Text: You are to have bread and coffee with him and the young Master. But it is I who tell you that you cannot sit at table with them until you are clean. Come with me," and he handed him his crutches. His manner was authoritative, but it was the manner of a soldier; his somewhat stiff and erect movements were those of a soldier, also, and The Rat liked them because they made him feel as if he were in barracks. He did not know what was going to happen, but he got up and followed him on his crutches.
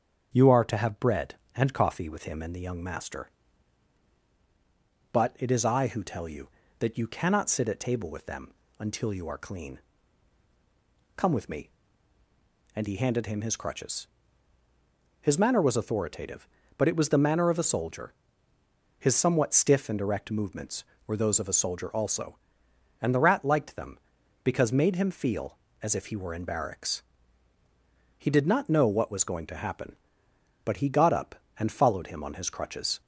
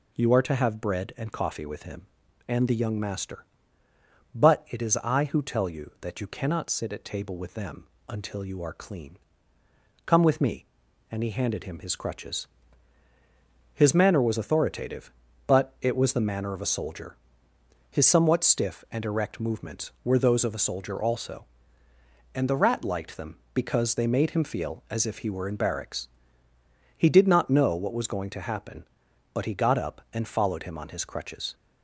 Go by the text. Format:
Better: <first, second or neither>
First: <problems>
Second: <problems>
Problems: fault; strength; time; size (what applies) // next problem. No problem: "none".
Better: second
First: starts louder than the rest; strong; until 1.3 s; 7 dB // pauses between "them" and "until"; slight; at 8.5 s; 0.28 s long // skips "they"; at 24.7 s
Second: pauses between "them" and "until"; slight; at 7.8 s; 0.22 s long